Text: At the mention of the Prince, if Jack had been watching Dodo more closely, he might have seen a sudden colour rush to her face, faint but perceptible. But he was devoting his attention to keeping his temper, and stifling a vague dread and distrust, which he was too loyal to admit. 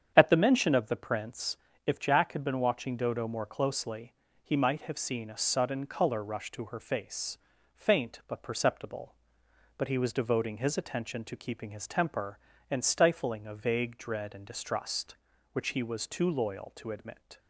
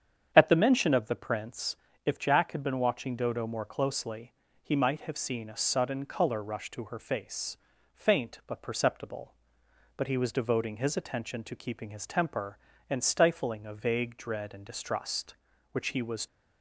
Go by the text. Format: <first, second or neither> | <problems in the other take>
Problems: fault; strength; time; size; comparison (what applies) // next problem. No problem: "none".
first | starts louder than the rest; strong; until 1.3 s; 8 dB; strong in the first // stops before "too loyal to admit"; at 16.2 s